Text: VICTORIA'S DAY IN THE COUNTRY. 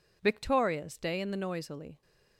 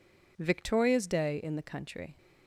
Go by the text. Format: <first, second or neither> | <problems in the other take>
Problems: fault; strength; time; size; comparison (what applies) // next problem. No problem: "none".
second | says "Noisily" for "COUNTRY"; at 1.3 s